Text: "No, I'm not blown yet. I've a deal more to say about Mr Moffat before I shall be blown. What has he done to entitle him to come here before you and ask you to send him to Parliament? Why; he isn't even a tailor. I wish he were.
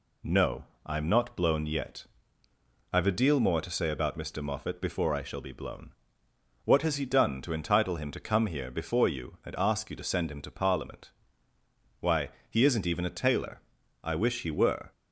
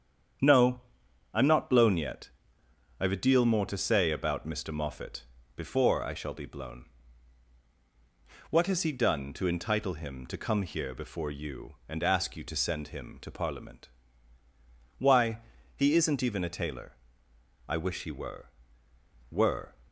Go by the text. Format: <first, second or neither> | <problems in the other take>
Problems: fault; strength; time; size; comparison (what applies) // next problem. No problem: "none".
first | starts louder than the rest; strong; until 1.9 s; 8.5 dB // pauses between "Moffat" and "before"; slight; at 5.2 s; 0.30 s long // says "were" twice; at 19.2 s